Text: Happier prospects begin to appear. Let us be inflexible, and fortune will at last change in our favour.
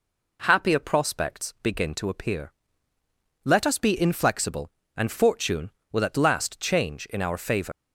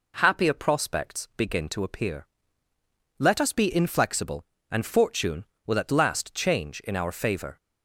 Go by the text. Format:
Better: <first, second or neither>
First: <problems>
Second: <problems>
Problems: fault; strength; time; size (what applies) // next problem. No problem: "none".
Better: second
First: leaves "favour" unfinished; at 7.7 s; 130 ms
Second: none